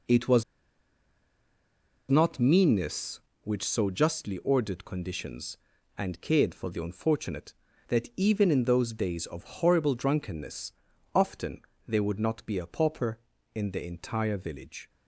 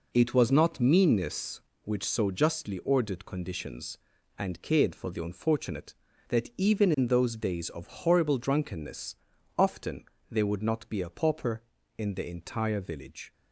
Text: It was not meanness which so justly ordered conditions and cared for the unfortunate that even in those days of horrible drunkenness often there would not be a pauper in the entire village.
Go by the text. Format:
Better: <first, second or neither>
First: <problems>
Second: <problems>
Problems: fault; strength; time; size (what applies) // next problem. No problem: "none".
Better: second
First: pauses between "was" and "not"; strong; at 0.4 s; 1.6 s long // pauses between "drunkenness" and "often"; at 10.7 s; 0.42 s long // pauses between "often" and "there"; slight; at 11.6 s; 0.24 s long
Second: pauses between "drunkenness" and "often"; at 9.1 s; 0.42 s long // pauses between "often" and "there"; slight; at 10.0 s; 0.24 s long